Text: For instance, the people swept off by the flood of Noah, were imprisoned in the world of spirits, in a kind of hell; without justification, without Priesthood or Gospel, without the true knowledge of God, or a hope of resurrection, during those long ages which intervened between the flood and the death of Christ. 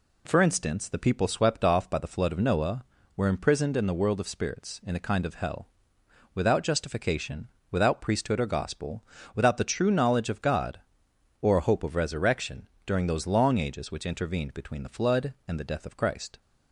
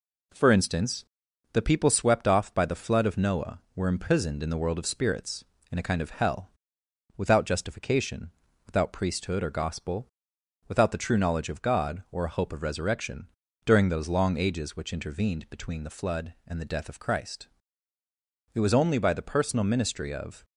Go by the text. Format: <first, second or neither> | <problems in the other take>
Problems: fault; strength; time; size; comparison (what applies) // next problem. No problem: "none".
first | goes on to say "It was only by the personal ministry of"; strong; from 18.5 s on; 1.9 s long